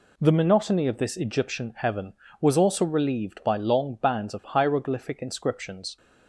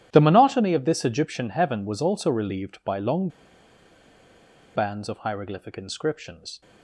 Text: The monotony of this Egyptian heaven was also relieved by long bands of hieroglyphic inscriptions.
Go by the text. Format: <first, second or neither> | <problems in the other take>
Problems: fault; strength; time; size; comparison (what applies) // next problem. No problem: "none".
first | pauses between "long" and "bands"; strong; at 3.2 s; 1.4 s long